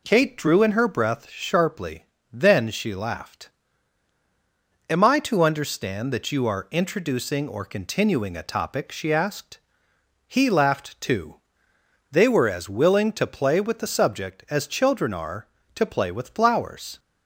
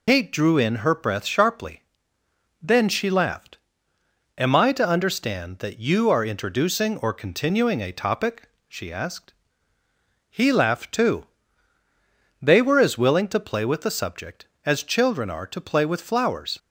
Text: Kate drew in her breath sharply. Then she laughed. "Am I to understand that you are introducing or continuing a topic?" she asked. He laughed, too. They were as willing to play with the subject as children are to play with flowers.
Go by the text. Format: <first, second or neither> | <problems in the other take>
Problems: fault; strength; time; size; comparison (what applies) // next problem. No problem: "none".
first | loses the start of "Kate"; at 0.0 s; 100 ms